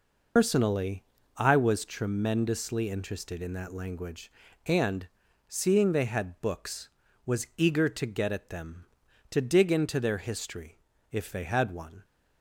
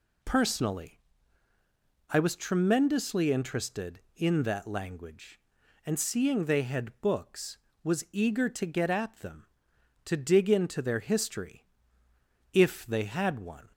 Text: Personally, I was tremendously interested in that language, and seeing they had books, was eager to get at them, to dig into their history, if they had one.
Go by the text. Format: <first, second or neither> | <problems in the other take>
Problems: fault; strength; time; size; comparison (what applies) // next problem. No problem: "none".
second | loses the start of "Personally"; at 0.3 s; 130 ms // pauses between "and" and "seeing"; at 5.0 s; 0.40 s long